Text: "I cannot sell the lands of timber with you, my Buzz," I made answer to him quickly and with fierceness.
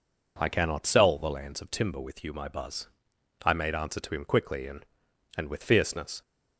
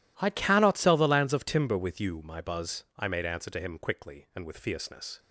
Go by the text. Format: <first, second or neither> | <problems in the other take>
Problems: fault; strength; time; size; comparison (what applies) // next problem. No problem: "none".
second | says "and" twice; at 5.3 s